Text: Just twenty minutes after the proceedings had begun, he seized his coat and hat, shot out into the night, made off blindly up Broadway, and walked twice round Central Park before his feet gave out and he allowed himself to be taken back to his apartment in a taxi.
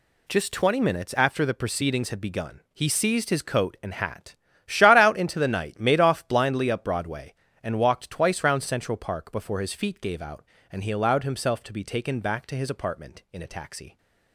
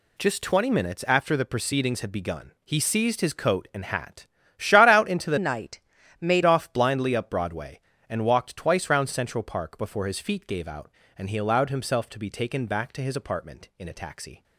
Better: first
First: none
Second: changes voice from "night" to "made"; from 5.3 to 6.4 s; 1.1 s long

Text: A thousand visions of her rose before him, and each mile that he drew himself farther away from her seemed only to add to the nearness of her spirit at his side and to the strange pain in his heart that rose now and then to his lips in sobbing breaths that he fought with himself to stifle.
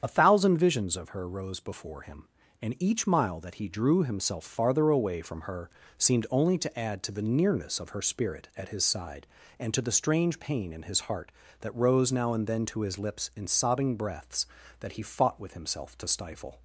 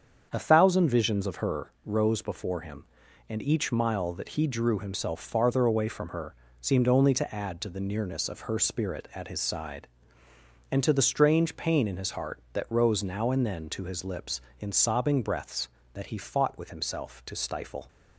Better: second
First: loses the start of "A"; at 0.0 s; 35 ms // starts louder than the rest; strong; until 1.0 s; 8 dB // pauses between "her" and "seemed"; slight; at 5.6 s; 0.30 s long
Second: starts louder than the rest; strong; until 1.3 s; 7.5 dB // pauses between "her" and "seemed"; slight; at 6.3 s; 0.26 s long

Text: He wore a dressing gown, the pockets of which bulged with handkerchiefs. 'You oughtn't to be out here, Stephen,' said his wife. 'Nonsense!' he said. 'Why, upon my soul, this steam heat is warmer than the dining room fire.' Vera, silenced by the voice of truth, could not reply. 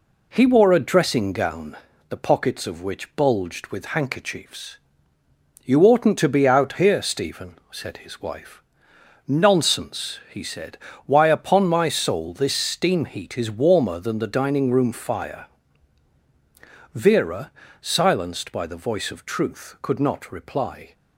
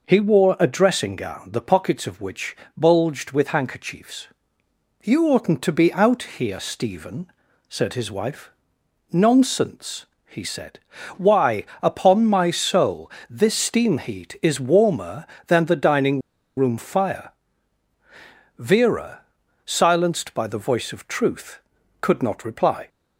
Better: first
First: none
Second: pauses between "which" and "bulged"; slight; at 2.5 s; 0.22 s long // pauses between "dining" and "room"; at 16.2 s; 0.36 s long

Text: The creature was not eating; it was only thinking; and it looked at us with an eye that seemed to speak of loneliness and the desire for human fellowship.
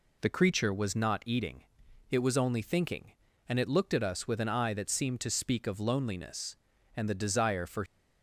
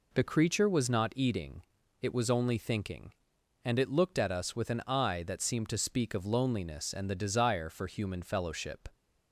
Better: second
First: stops before "human fellowship"; at 7.8 s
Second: none

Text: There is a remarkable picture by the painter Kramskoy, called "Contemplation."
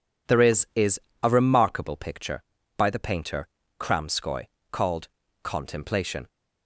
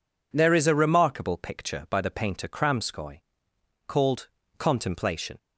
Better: second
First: says "is" twice; at 0.7 s // pauses between "painter" and "Kramskoy"; slight; at 3.4 s; 0.32 s long // pauses between "called" and "Contemplation"; slight; at 5.0 s; 0.34 s long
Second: pauses between "called" and "Contemplation"; slight; at 4.2 s; 0.28 s long

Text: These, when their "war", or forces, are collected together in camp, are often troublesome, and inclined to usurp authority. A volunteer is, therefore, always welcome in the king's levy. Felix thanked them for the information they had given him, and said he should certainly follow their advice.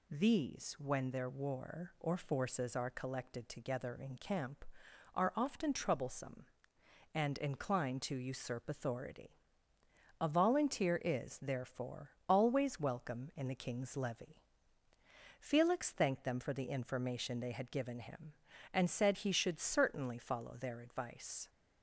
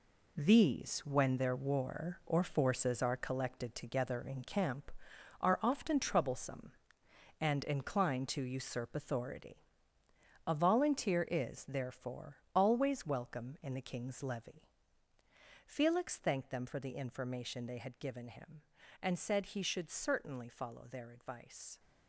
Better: first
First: none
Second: gets quieter; strong; throughout; 9 dB

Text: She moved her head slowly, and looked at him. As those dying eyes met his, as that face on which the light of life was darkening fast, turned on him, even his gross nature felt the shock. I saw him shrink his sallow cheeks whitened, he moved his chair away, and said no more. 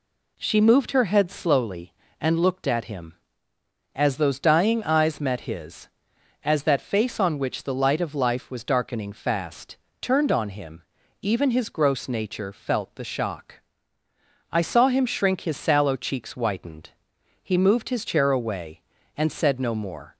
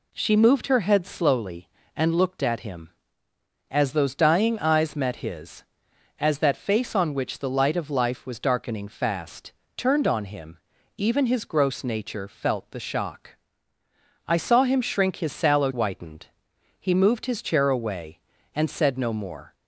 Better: first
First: none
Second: skips "cheeks"; at 15.7 s

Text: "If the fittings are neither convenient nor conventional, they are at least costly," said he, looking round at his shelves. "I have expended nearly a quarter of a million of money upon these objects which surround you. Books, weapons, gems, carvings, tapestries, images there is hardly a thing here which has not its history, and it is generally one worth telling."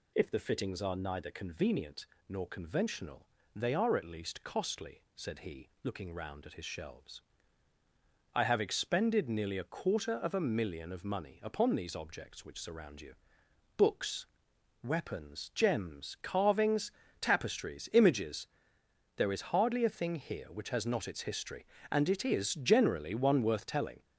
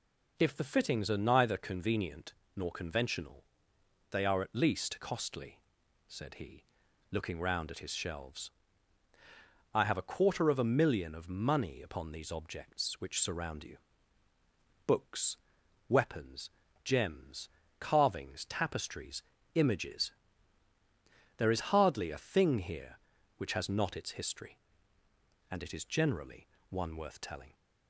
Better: first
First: pauses between "convenient" and "nor"; slight; at 2.0 s; 0.24 s long // pauses between "images" and "there"; noticeable; at 18.4 s; 0.70 s long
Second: pauses between "convenient" and "nor"; slight; at 2.3 s; 0.22 s long // skips "expended nearly"; at 9.9 s // pauses between "images" and "there"; strong; at 20.1 s; 1.2 s long // pauses between "generally" and "one"; slight; at 26.4 s; 0.22 s long

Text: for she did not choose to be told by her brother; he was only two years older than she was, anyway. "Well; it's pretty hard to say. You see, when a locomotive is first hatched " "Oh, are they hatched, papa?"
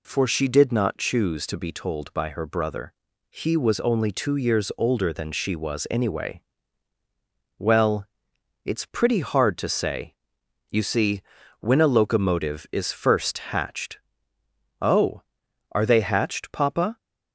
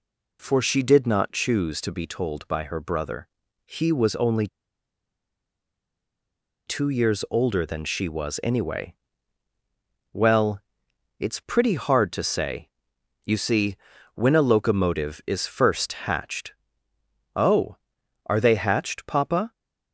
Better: first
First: none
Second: pauses between "only" and "two"; strong; at 4.4 s; 2.2 s long

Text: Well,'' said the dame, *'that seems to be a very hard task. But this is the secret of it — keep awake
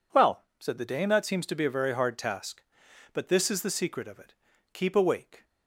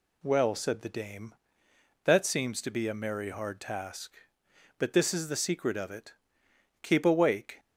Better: first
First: none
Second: says "merry" for "very"; at 2.9 s

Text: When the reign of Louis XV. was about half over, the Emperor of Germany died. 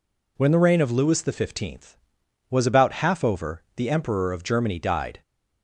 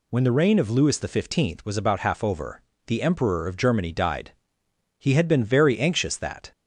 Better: first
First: none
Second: goes on to say "He had been very anxious that"; from 4.9 s on; 1.5 s long

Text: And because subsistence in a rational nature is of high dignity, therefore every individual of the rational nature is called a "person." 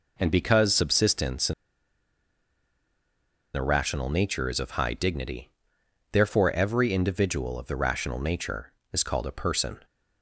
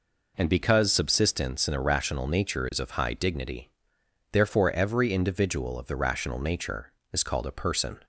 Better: second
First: pauses between "in" and "a"; strong; at 1.5 s; 2.0 s long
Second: none

